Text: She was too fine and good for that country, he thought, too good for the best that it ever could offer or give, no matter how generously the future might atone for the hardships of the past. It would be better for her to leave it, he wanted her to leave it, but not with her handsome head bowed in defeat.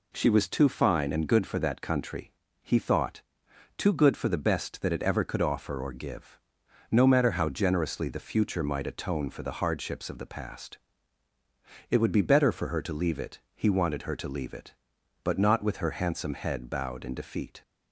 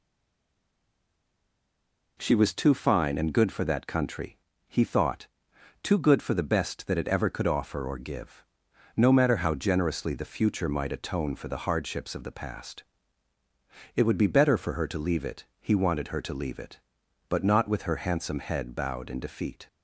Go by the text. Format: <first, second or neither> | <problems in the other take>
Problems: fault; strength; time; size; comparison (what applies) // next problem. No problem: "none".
first | stays silent before the first word; until 2.1 s; 2.1 s long